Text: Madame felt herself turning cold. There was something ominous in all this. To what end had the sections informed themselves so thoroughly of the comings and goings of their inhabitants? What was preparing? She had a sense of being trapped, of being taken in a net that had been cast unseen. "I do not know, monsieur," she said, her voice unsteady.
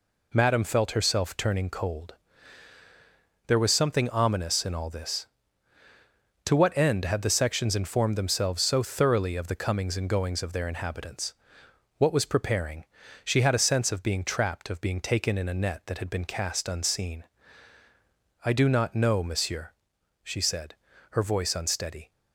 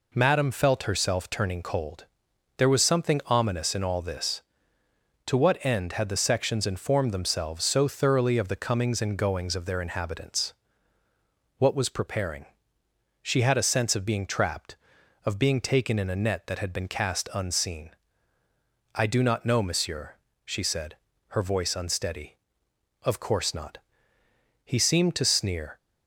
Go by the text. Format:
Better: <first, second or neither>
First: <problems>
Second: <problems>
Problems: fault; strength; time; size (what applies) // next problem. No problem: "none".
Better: first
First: none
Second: goes on to say "Of course not He seemed to sneer"; strong; from 23.0 s on; 2.7 s long